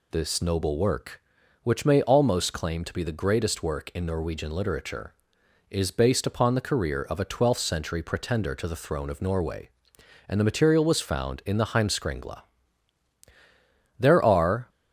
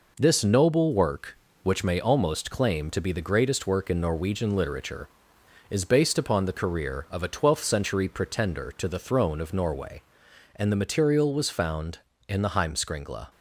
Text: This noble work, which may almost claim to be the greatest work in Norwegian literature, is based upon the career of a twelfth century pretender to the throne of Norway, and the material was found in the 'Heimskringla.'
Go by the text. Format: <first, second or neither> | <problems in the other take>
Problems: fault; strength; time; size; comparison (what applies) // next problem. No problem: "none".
second | goes on to say "There are"; noticeable; from 13.9 s on; 0.70 s long